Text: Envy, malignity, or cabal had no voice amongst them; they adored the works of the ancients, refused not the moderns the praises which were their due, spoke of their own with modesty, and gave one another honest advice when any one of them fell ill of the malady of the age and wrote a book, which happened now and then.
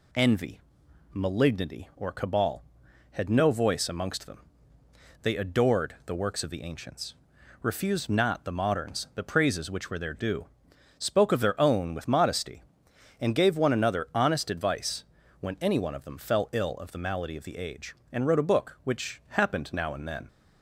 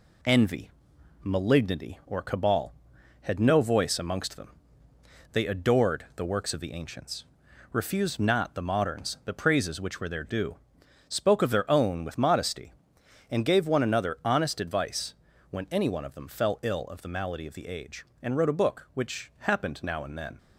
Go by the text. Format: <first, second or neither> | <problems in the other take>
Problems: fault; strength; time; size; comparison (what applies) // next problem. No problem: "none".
first | gets quieter; throughout; 3.5 dB // pauses between "advice" and "when"; slight; at 15.1 s; 0.34 s long; slight in the first